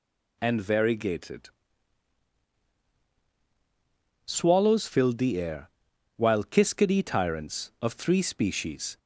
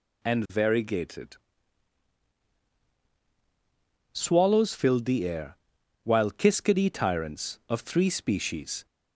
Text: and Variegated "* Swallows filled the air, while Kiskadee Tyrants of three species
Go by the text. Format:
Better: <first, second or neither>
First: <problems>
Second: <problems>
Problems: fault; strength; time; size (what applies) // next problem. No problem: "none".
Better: neither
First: none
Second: none